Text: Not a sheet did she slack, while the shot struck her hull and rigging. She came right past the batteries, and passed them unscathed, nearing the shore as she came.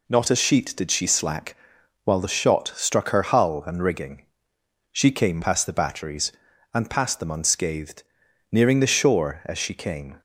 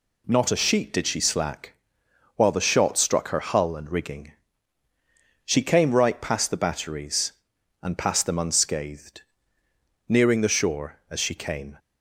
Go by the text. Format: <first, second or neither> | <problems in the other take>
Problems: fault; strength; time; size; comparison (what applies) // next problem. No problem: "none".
second | skips "right"; at 5.4 s